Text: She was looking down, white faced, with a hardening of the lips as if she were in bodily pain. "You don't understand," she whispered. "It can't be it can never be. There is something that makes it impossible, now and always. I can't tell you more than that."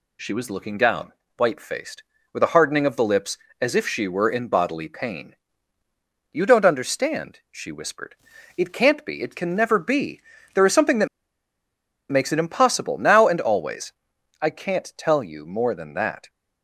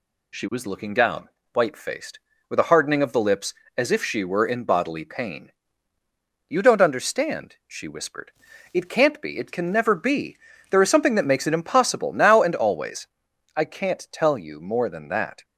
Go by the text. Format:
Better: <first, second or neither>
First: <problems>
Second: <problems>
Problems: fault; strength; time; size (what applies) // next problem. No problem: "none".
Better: second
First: pauses between "that" and "makes"; at 11.0 s; 1.0 s long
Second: none